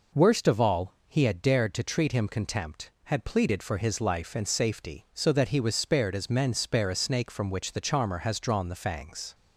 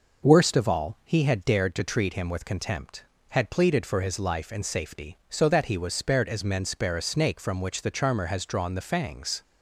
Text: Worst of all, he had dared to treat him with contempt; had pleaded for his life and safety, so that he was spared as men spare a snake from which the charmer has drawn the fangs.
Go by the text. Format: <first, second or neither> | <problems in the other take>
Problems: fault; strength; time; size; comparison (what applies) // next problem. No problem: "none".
second | skips "with"; at 2.2 s